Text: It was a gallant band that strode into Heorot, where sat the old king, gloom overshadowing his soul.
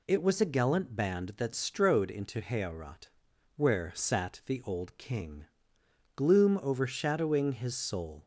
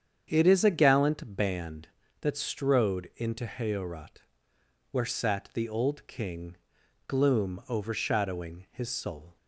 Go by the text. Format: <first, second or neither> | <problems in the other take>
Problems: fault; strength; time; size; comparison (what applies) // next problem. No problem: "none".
first | starts louder than the rest; strong; until 1.2 s; 8 dB // says "is" for "was"; at 0.4 s